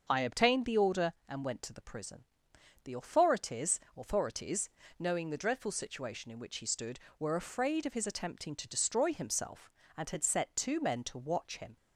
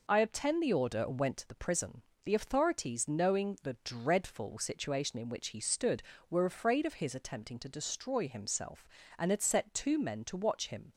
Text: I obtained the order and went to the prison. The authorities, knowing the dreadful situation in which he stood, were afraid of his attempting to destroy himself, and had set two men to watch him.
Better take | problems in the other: second | starts louder than the rest; until 1.1 s; 6.5 dB // says "authorities" twice; at 3.9 s

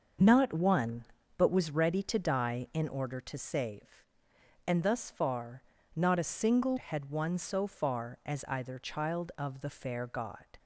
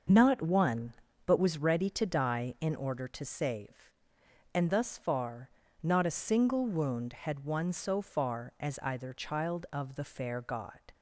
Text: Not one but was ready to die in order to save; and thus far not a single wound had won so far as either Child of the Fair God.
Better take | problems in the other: second | starts louder than the rest; until 1.5 s; 6 dB; noticeable in the second // pauses between "far" and "not"; slight; at 5.6 s; 0.34 s long; slight in the second // skips "wound"; at 6.7 s

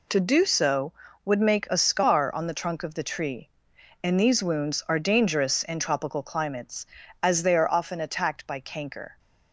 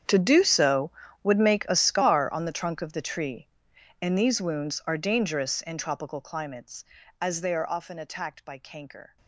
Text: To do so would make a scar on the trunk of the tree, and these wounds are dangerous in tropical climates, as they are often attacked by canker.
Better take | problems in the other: first | gets quieter; strong; throughout; 20 dB

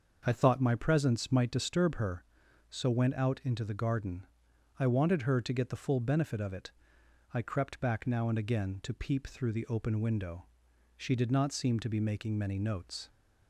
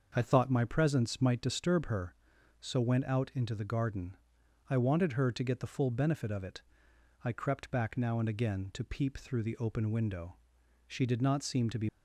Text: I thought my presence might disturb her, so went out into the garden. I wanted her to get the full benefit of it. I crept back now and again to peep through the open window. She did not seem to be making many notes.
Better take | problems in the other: first | starts louder than the rest; until 1.1 s; 6.5 dB; also in the first // stops before "making many notes"; at 11.8 s

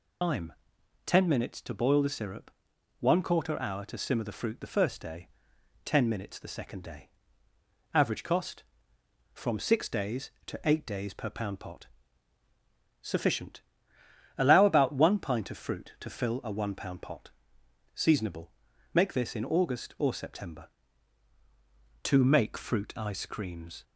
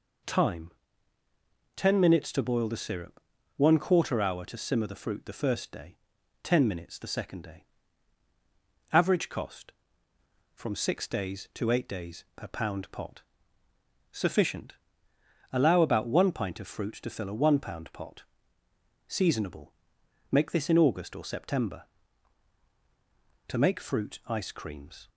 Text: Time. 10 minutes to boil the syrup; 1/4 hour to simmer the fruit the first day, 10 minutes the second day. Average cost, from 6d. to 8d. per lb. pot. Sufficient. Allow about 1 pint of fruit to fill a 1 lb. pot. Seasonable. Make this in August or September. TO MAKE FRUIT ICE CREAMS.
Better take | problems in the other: second | loses the start of "Time"; at 0.2 s; 100 ms

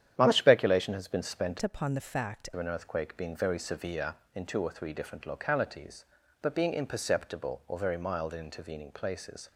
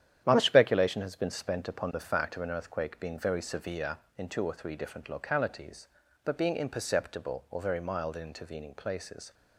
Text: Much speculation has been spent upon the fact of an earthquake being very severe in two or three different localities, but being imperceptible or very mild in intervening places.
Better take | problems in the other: second | starts louder than the rest; strong; until 1.1 s; 10 dB; strong in the second // changes voice from "upon" to "fact"; from 1.6 to 2.4 s; 0.8 s long

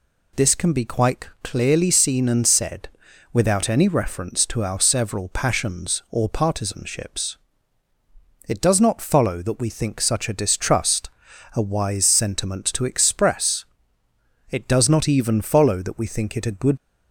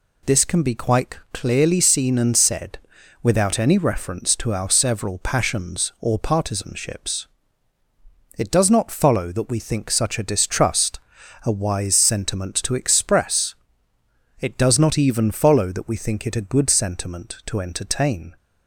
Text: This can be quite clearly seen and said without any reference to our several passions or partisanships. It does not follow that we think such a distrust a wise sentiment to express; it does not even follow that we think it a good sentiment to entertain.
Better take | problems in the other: second | pauses between "said" and "without"; at 2.8 s; 0.44 s long; also in the second // pauses between "distrust" and "a"; noticeable; at 11.1 s; 0.46 s long; noticeable in the second // stops before "sentiment to entertain"; at 16.7 s

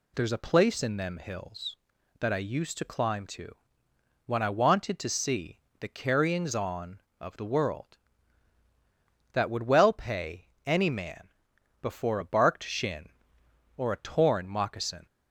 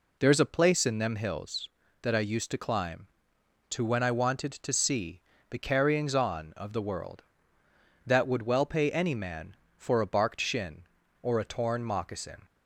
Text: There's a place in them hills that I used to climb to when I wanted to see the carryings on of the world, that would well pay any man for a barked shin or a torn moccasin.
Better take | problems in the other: second | pauses between "to" and "when"; noticeable; at 3.5 s; 0.74 s long // pauses between "see" and "the"; slight; at 5.5 s; 0.22 s long; slight in the second // pauses between "pay" and "any"; slight; at 10.4 s; 0.20 s long // says "before" for "for"; at 11.8 s

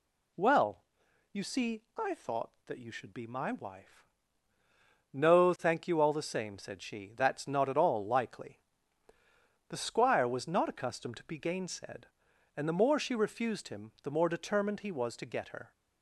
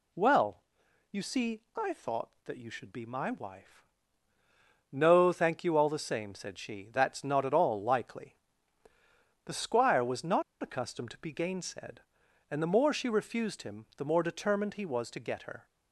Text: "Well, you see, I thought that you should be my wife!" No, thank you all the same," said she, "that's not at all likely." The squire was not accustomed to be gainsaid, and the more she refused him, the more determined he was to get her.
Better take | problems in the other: first | pauses between "not" and "accustomed"; slight; at 10.4 s; 0.18 s long

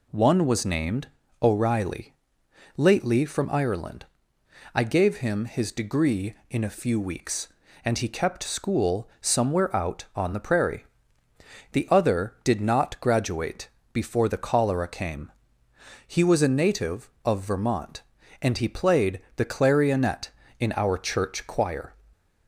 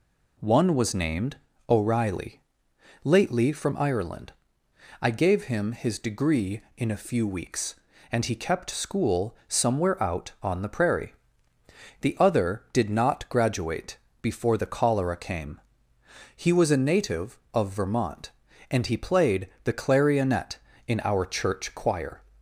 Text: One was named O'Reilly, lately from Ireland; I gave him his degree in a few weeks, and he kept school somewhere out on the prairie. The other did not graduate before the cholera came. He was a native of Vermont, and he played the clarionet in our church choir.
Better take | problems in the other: neither | pauses between "named" and "O'Reilly"; slight; the same in both // pauses between "graduate" and "before"; slight; the same in both // pauses between "played" and "the"; slight; the same in both

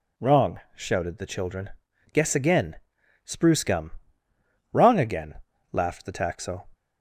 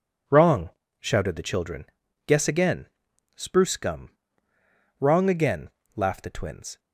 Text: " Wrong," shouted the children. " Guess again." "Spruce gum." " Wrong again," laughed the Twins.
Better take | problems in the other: second | says "Taxo" for "Twins"; at 6.1 s

